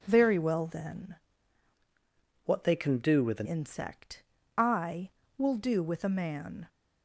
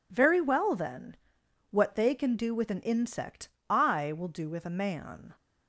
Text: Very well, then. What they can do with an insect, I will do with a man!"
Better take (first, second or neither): second